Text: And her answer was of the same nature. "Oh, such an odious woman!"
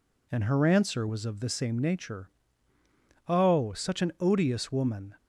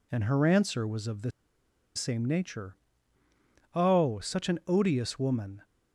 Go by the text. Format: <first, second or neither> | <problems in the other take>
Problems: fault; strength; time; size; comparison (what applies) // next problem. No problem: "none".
first | pauses between "the" and "same"; noticeable; at 1.3 s; 0.64 s long